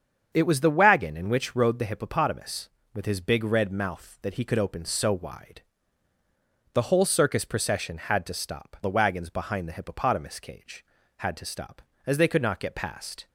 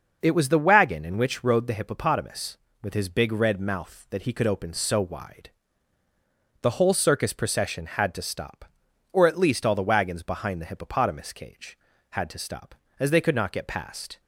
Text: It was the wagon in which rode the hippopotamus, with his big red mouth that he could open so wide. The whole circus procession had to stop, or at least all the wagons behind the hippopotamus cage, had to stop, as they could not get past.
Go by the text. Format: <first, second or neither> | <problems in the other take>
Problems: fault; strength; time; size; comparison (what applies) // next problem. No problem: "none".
second | starts louder than the rest; strong; until 1.3 s; 7.5 dB // skips "or at least all"; at 8.8 s